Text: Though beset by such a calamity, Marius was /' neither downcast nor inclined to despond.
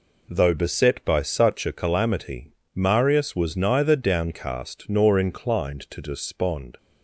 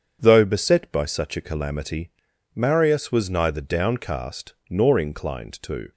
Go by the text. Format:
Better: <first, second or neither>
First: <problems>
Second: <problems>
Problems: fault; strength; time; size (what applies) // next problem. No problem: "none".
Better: first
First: none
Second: starts louder than the rest; strong; until 1.2 s; 7.5 dB // pauses between "downcast" and "nor"; slight; at 4.5 s; 0.16 s long // stops before "despond"; at 5.9 s